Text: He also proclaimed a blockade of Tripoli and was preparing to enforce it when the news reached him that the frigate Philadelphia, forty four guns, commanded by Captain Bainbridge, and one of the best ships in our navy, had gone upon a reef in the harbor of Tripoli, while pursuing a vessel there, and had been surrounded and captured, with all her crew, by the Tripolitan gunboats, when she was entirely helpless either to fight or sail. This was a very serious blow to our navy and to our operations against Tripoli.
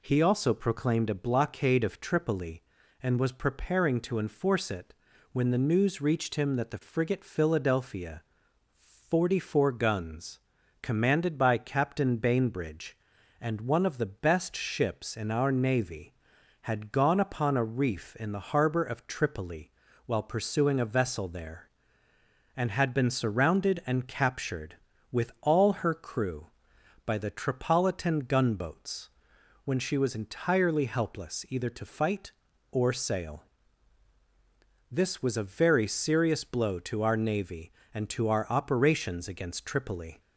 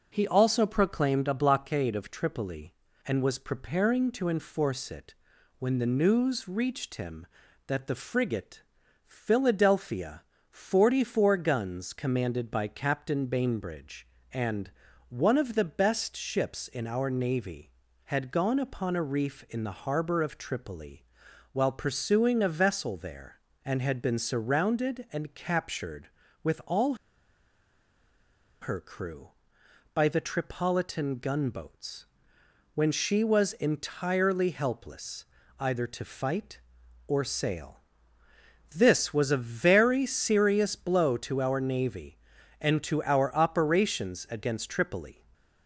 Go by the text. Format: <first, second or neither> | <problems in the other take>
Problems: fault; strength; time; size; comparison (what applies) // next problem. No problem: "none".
first | pauses between "it" and "when"; at 5.1 s; 0.42 s long; also in the first // pauses between "frigate" and "Philadelphia"; noticeable; at 8.6 s; 0.46 s long // pauses between "and" and "one"; at 14.6 s; 0.40 s long // pauses between "all" and "her"; strong; at 26.9 s; 1.6 s long // pauses between "helpless" and "either"; slight; at 35.2 s; 0.34 s long